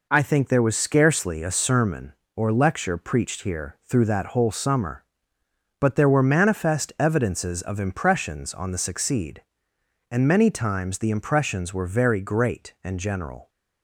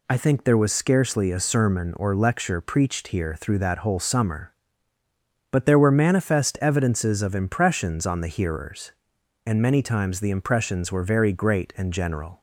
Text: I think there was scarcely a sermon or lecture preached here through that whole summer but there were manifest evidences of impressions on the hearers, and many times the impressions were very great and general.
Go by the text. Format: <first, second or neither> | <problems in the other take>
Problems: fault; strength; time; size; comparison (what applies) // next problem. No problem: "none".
second | says "succeed" for "hearers"; at 8.7 s